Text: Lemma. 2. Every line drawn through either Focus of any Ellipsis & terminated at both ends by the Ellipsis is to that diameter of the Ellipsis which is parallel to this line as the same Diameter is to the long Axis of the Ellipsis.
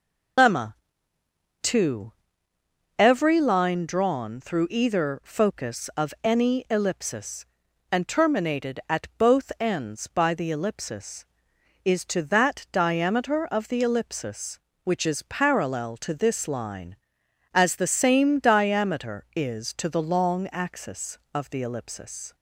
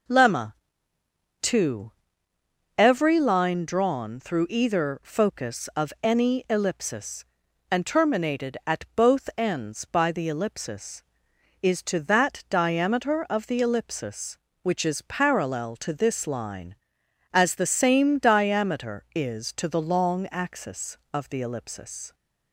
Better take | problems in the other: second | loses the start of "Lemma"; at 0.3 s; 90 ms // starts louder than the rest; until 3.1 s; 6.5 dB

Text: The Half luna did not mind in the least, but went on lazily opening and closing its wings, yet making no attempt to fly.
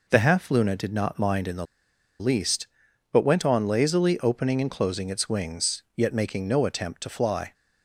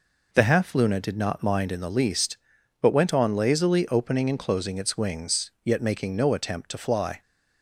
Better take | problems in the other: second | pauses between "the" and "least"; noticeable; at 1.6 s; 0.55 s long

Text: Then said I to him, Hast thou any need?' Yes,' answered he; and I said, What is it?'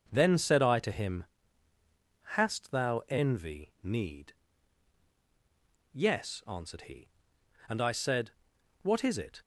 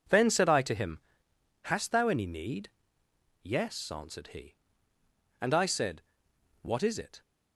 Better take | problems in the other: second | says "envy" for "any"; at 3.0 s

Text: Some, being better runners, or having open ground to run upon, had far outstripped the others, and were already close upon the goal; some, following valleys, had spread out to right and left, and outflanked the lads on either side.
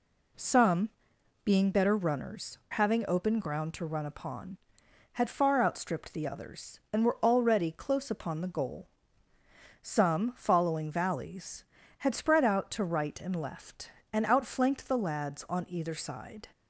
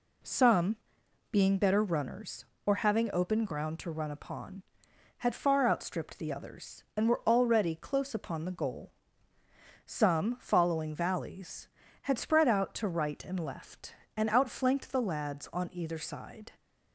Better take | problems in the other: second | skips "or"; at 2.6 s

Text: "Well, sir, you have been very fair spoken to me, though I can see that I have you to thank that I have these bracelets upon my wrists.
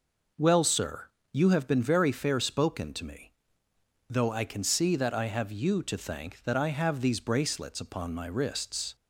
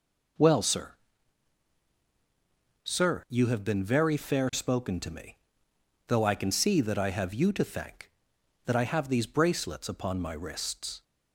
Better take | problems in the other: first | says "sir" twice; at 2.8 s

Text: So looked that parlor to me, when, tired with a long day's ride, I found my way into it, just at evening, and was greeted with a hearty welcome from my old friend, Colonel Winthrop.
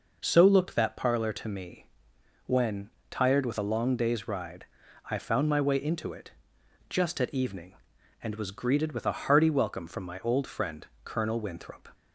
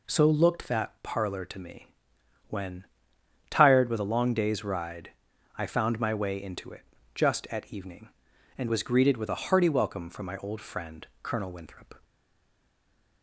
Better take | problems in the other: first | stays silent after the last word; noticeable; from 12.0 s on; 1.2 s long

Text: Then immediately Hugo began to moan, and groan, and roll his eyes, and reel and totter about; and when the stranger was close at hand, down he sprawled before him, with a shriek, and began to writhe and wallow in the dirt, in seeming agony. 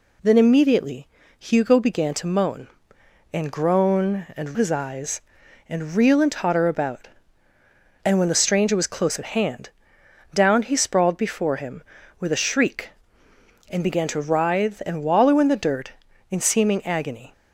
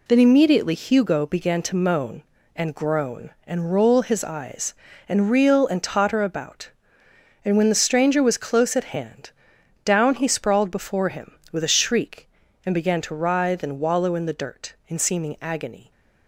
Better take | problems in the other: second | pauses between "immediately" and "Hugo"; slight; at 1.0 s; 0.32 s long // skips "roll"; at 4.5 s

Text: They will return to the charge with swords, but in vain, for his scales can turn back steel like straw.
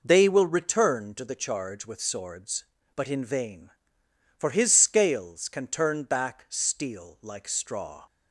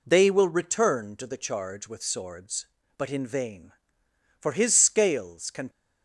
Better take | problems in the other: first | stops before "turn back steel like straw"; at 5.6 s

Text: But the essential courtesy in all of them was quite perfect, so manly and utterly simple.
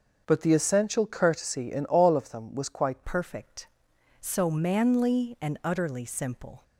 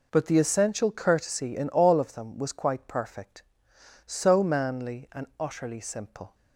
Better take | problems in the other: second | starts louder than the rest; until 1.2 s; 6.5 dB // changes voice at "perfect"; from 3.0 s on; 3.6 s long

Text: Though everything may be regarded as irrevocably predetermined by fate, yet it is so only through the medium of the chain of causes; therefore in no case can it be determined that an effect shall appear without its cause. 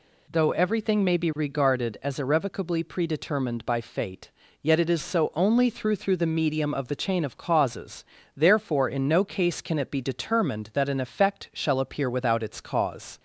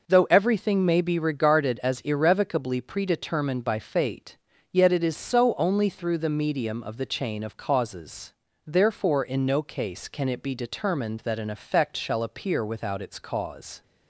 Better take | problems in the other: second | says "through" twice; at 5.9 s

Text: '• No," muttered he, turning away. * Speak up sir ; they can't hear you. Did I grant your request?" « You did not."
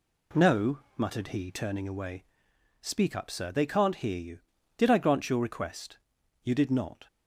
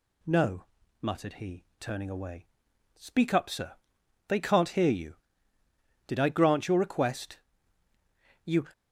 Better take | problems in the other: first | stops before "did not"; at 8.7 s

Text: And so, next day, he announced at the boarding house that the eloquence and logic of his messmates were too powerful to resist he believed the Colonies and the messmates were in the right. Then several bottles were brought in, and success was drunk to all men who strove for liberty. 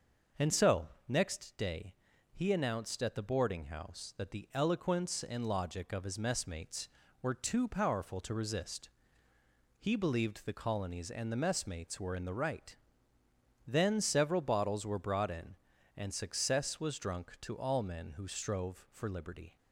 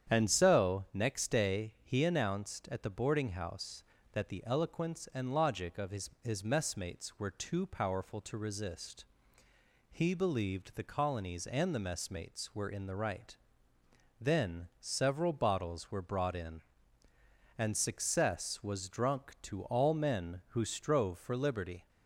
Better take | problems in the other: first | starts louder than the rest; strong; until 1.1 s; 9 dB; also in the first // says "his" twice; at 6.2 s // pauses between "resist" and "he"; noticeable; at 9.0 s; 0.88 s long; noticeable in the first

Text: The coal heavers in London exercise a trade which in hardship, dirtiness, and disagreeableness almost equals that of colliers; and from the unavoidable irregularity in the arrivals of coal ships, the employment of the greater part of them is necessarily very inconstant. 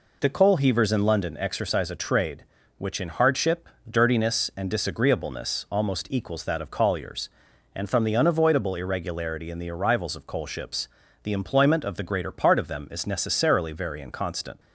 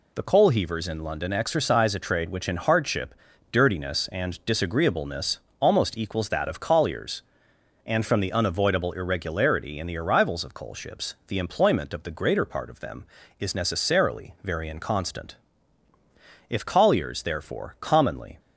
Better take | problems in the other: first | pauses between "disagreeableness" and "almost"; slight; at 5.3 s; 0.22 s long // goes on to say "If colliers therefore commonly"; strong; from 16.4 s on; 1.9 s long

